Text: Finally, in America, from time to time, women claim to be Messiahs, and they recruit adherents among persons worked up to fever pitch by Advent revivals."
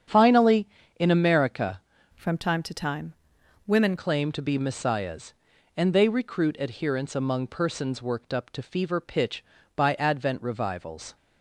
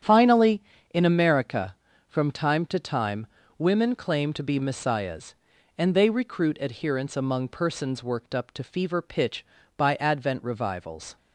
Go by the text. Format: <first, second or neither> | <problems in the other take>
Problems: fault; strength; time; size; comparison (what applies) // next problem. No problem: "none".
second | starts louder than the rest; strong; until 1.4 s; 8.5 dB; strong in the second // changes voice from "from" to "women"; from 2.1 to 3.9 s; 1.8 s long